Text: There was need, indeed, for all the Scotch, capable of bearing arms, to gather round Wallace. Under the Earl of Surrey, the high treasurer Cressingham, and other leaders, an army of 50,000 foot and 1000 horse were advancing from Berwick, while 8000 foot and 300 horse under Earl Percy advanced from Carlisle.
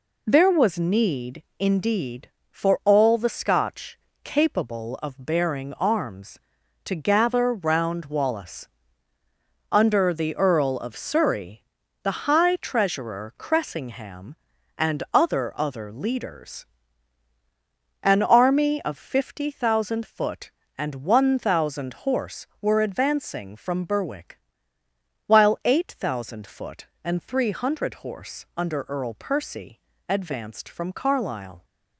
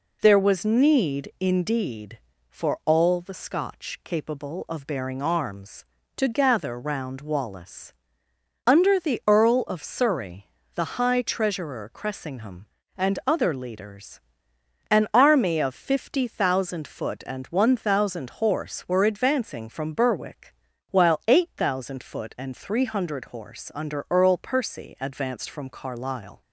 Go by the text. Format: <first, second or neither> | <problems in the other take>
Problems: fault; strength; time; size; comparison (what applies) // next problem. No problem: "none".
second | says "other" twice; at 15.5 s // pauses between "Percy" and "advanced"; slight; at 29.8 s; 0.26 s long